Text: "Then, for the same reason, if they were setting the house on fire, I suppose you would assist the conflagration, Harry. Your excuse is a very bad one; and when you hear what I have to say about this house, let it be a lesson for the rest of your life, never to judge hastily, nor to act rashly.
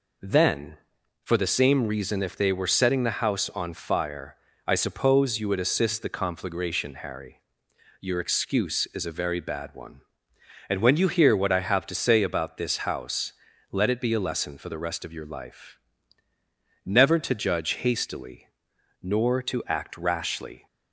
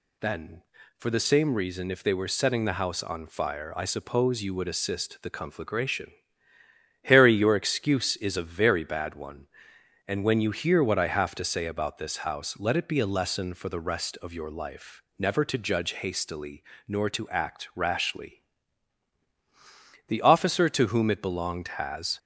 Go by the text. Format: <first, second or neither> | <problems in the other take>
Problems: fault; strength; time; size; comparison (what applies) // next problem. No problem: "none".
first | goes on to say "The officer to whom it belonged has"; strong; from 20.0 s on; 2.1 s long